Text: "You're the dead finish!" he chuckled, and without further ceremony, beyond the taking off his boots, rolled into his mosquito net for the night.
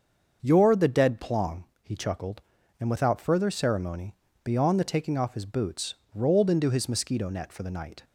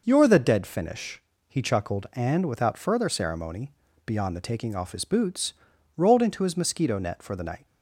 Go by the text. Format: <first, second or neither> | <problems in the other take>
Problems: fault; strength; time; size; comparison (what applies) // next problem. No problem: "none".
second | starts louder than the rest; until 1.4 s; 6.5 dB // says "plong" for "finish"; at 1.1 s